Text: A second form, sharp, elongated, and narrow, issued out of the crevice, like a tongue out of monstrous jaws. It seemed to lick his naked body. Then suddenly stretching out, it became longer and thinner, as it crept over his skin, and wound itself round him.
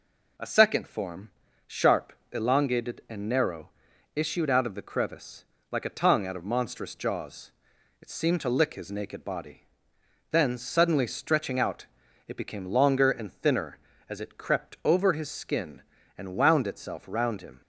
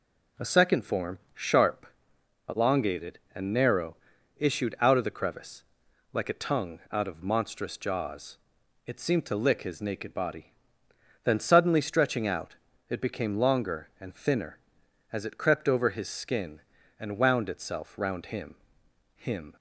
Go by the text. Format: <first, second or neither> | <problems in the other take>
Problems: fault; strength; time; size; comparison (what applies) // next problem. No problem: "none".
first | says "him" twice; at 19.1 s